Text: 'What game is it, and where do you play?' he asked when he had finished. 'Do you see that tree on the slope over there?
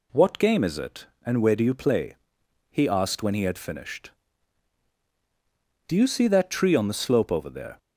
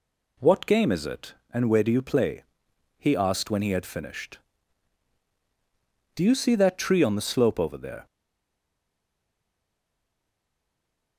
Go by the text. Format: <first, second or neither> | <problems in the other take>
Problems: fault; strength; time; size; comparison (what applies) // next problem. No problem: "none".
first | stays silent after the last word; strong; from 8.0 s on; 3.1 s long